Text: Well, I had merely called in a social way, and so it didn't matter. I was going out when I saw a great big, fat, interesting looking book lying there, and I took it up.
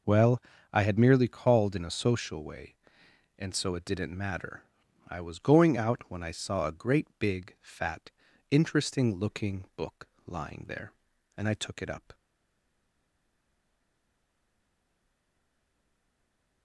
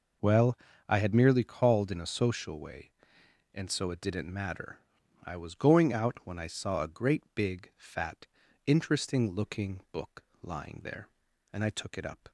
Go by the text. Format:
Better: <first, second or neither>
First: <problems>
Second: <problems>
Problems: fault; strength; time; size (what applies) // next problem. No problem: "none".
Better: second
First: pauses between "book" and "lying"; slight; at 10.0 s; 0.20 s long // stays silent after the last word; strong; from 12.1 s on; 4.5 s long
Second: pauses between "book" and "lying"; slight; at 10.2 s; 0.20 s long